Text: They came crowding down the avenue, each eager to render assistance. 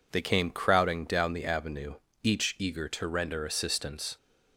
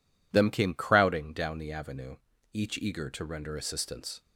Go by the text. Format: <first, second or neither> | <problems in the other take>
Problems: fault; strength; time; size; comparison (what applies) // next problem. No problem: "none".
first | says "Them" for "They"; at 0.3 s